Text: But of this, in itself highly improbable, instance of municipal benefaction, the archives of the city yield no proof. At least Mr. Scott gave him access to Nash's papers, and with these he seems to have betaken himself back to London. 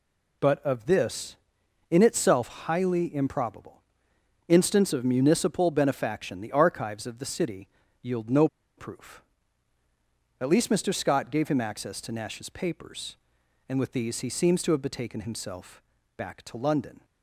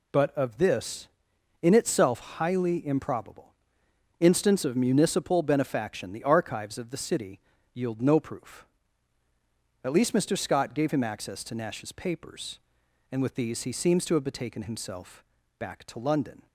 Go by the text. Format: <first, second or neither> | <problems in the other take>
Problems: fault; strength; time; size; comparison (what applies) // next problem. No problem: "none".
second | pauses between "city" and "yield"; slight; at 7.6 s; 0.34 s long; slight in the second // pauses between "no" and "proof"; slight; at 8.4 s; 0.31 s long // pauses between "himself" and "back"; slight; at 15.8 s; 0.36 s long; slight in the second